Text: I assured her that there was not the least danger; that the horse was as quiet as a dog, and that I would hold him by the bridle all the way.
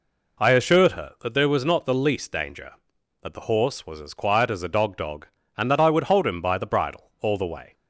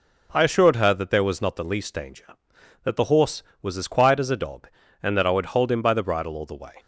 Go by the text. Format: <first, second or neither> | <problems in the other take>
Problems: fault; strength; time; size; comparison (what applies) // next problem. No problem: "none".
second | says "dog" twice; at 4.9 s